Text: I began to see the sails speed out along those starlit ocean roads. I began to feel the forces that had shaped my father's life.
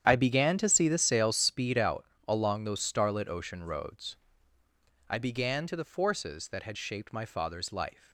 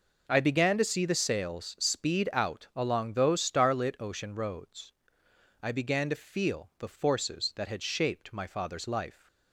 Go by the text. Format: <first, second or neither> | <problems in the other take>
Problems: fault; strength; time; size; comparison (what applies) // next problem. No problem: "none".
second | starts louder than the rest; strong; until 1.1 s; 9 dB // pauses between "out" and "along"; slight; at 2.0 s; 0.24 s long // skips "feel"; at 5.7 s